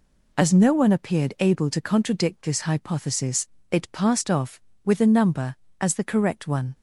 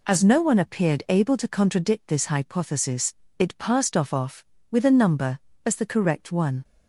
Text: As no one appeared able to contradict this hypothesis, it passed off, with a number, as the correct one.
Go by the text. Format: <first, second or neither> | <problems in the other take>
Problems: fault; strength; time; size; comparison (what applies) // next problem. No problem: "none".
first | says "off" twice; at 4.1 s